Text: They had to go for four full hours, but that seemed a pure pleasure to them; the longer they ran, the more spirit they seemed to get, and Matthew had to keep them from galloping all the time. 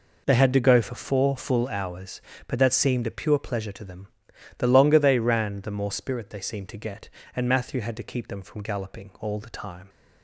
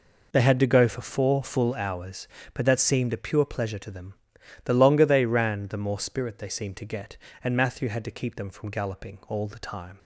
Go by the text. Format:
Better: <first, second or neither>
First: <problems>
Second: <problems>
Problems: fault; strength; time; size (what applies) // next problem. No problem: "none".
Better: neither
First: none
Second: none